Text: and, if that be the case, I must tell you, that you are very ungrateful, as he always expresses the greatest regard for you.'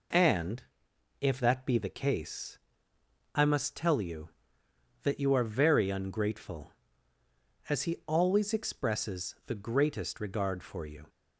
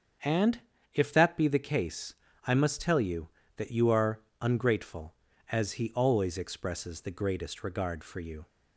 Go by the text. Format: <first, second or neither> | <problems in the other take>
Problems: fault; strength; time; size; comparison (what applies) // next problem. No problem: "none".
first | starts louder than the rest; strong; until 1.5 s; 7.5 dB // skips "very"; at 4.3 s